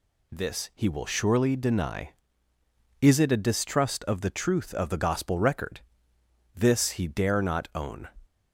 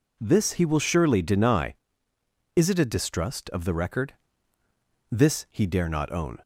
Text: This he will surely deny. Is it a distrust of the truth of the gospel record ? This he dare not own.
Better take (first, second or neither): first